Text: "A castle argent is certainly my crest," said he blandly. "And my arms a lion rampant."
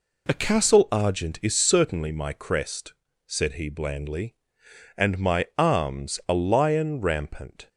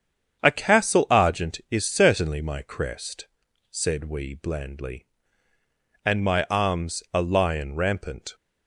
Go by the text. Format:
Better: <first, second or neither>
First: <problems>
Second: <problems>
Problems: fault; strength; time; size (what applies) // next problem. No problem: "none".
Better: first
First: none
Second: starts louder than the rest; strong; until 1.4 s; 8 dB // says "we" for "he"; at 4.0 s